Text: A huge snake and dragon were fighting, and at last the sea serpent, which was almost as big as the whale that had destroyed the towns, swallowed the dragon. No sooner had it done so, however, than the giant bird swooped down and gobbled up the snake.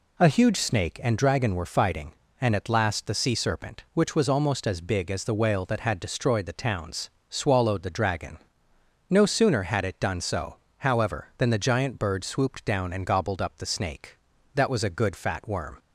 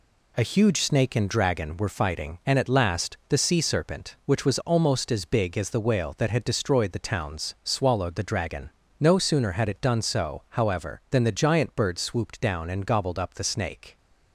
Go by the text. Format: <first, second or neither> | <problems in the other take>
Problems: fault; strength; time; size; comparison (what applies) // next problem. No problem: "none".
second | goes on to say "That was a good fat worm"; noticeable; from 14.5 s on; 1.2 s long